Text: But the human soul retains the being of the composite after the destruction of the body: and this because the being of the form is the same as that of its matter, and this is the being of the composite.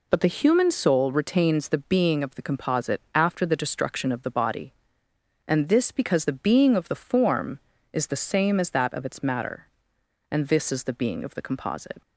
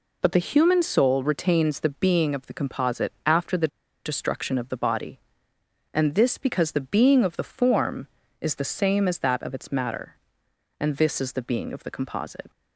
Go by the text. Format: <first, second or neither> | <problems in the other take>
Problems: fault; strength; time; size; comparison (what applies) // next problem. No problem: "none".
first | pauses between "the" and "destruction"; at 3.6 s; 0.37 s long